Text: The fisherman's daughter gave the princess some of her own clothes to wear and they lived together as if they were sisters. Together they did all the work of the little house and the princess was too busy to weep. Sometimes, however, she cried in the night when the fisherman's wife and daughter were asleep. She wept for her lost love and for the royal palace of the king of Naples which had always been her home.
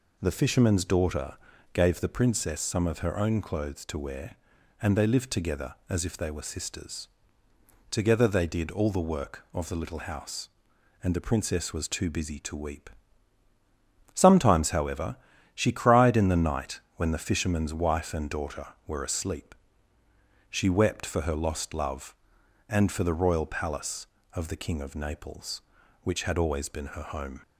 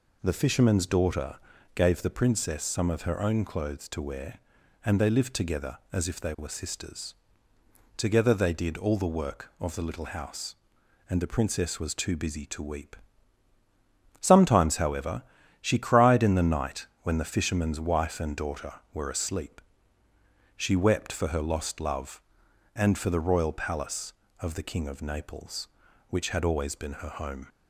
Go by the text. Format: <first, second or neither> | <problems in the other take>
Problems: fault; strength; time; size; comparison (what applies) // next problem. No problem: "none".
neither | pauses between "daughter" and "gave"; the same in both // pauses between "night" and "when"; slight; the same in both